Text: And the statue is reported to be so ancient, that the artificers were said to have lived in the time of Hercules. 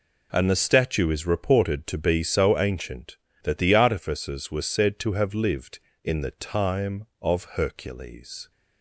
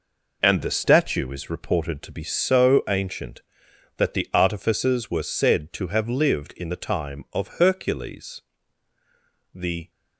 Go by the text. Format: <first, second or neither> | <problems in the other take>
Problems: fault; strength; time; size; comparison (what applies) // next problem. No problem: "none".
first | goes on to say "The"; slight; from 9.5 s on; 0.36 s long